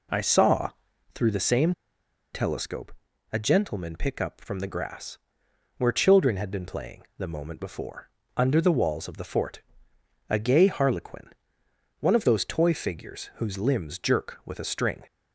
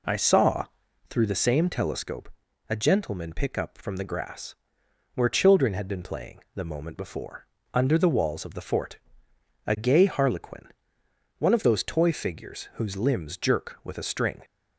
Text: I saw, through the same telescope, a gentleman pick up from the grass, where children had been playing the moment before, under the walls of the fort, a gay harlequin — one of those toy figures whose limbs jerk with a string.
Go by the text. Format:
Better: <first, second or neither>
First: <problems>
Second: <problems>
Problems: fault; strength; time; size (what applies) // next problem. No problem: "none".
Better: second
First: pauses between "same" and "telescope"; noticeable; at 1.7 s; 0.61 s long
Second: none